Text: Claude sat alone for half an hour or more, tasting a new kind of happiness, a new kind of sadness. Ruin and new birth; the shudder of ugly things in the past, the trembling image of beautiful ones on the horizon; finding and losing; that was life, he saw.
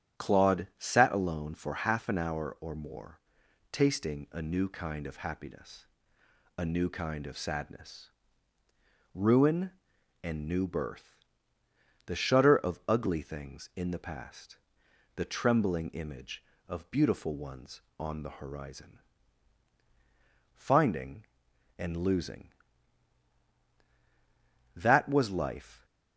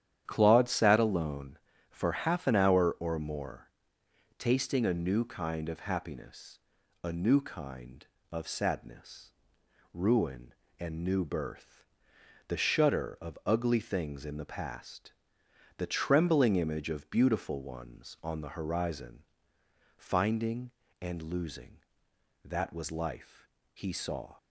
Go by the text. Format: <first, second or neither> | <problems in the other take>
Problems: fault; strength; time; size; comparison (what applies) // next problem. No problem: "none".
second | starts louder than the rest; strong; until 1.2 s; 9.5 dB; strong in the second // stops before "he saw"; at 25.8 s